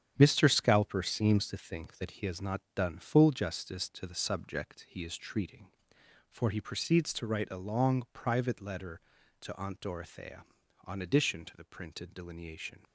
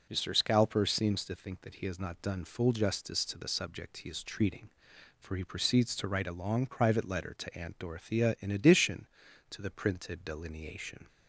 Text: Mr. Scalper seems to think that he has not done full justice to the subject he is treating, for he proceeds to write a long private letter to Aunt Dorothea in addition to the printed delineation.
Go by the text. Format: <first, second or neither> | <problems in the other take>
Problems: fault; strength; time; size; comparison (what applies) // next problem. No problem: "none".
second | starts louder than the rest; strong; until 1.1 s; 9 dB // says "on" for "in"; at 10.8 s